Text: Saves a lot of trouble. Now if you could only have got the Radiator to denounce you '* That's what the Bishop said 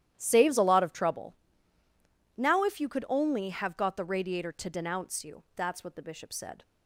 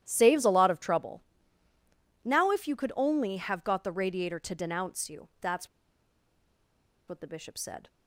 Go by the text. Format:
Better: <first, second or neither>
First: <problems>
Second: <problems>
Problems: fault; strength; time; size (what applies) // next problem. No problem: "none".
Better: first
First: starts louder than the rest; strong; until 1.1 s; 12 dB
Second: starts louder than the rest; strong; until 1.0 s; 12 dB // pauses between "That's" and "what"; strong; at 5.6 s; 1.3 s long